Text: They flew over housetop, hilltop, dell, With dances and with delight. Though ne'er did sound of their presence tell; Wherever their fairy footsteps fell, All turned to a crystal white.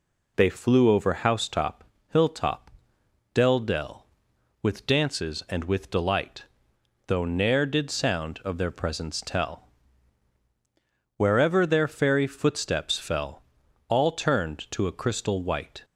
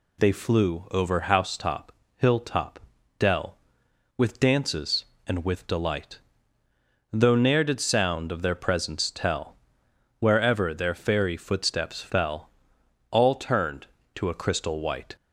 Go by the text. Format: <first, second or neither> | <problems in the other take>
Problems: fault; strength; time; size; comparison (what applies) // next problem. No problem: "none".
second | says "dell" twice; at 3.5 s